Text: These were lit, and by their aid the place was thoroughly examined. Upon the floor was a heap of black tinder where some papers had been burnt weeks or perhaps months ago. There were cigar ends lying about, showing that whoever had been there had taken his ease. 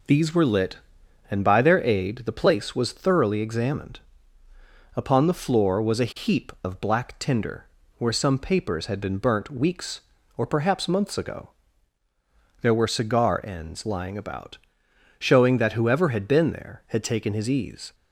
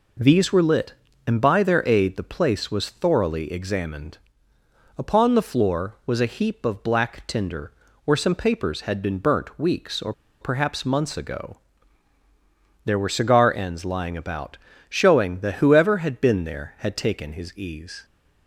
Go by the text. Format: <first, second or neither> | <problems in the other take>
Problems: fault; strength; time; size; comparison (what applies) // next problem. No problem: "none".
first | pauses between "tinder" and "where"; slight; at 7.6 s; 0.34 s long; slight in the first // pauses between "or" and "perhaps"; slight; at 10.1 s; 0.29 s long